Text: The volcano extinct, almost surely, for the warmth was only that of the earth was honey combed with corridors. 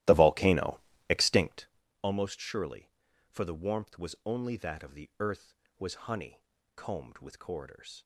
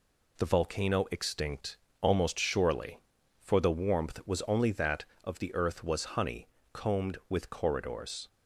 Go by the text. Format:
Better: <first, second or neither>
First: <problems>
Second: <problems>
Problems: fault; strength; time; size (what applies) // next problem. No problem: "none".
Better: second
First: starts louder than the rest; strong; until 1.9 s; 15 dB // pauses between "volcano" and "extinct"; slight; at 0.7 s; 0.30 s long // pauses between "honey" and "combed"; slight; at 6.4 s; 0.32 s long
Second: pauses between "honey" and "combed"; slight; at 6.4 s; 0.26 s long